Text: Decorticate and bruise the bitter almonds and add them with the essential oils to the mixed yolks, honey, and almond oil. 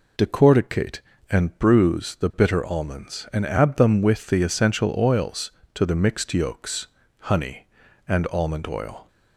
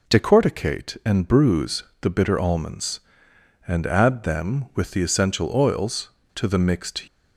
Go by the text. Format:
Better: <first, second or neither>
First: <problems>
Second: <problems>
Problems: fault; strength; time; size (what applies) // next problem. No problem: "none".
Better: first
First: none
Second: pauses between "bruise" and "the"; slight; at 1.8 s; 0.20 s long // stops before "yolks honey and almond oil"; at 7.0 s